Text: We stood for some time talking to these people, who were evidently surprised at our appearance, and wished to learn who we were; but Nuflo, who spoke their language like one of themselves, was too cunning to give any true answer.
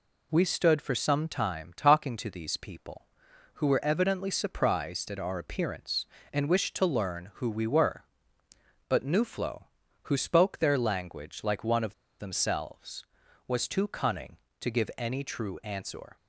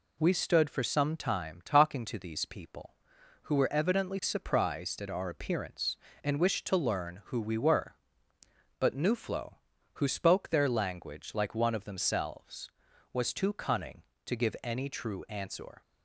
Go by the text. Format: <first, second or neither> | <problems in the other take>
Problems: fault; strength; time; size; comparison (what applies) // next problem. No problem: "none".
second | pauses between "of" and "themselves"; slight; at 11.9 s; 0.25 s long